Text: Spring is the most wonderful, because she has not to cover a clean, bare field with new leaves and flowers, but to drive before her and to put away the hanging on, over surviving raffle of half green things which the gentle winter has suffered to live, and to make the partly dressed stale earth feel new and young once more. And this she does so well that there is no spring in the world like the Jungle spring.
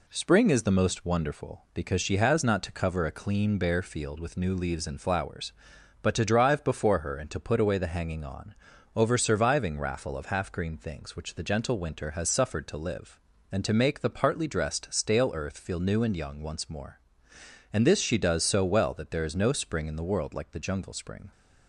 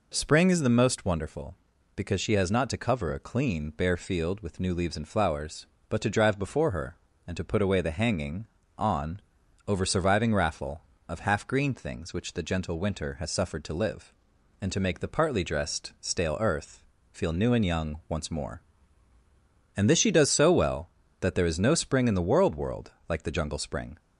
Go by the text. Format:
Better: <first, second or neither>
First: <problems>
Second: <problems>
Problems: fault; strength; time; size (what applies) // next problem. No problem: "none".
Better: first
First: none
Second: pauses between "earth" and "feel"; slight; at 16.8 s; 0.30 s long // says "world" twice; at 22.5 s